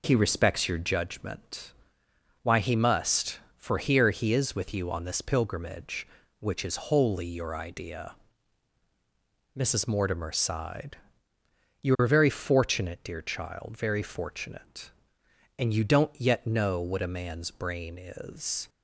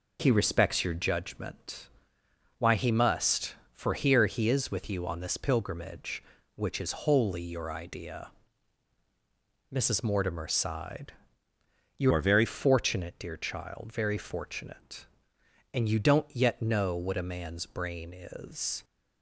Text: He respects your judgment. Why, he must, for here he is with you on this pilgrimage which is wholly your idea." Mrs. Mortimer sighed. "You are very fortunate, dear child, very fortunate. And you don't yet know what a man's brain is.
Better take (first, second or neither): first